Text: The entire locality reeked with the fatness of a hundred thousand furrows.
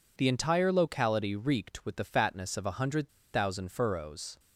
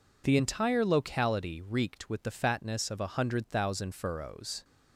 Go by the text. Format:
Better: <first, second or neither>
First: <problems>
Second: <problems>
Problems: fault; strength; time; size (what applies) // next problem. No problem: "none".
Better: second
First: pauses between "hundred" and "thousand"; slight; at 3.1 s; 0.23 s long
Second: none